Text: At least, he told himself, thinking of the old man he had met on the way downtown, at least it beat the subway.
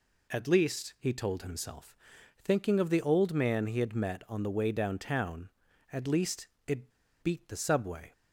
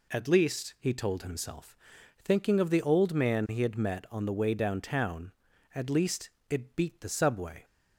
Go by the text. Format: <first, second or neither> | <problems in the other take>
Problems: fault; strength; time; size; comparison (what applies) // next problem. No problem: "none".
second | pauses between "least" and "it"; slight; at 6.4 s; 0.18 s long; slight in the second // pauses between "it" and "beat"; slight; at 6.9 s; 0.32 s long